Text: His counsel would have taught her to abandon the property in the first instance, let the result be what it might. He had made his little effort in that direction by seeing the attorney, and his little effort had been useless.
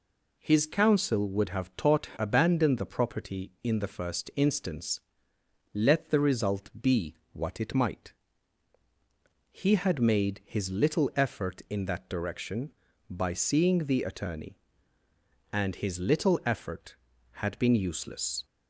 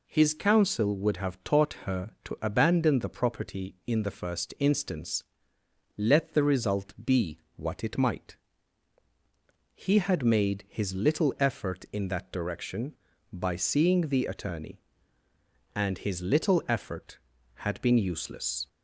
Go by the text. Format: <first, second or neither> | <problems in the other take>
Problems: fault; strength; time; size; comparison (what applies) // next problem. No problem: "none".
second | skips "her to"; at 2.1 s // pauses between "be" and "what"; slight; at 7.1 s; 0.16 s long; slight in the second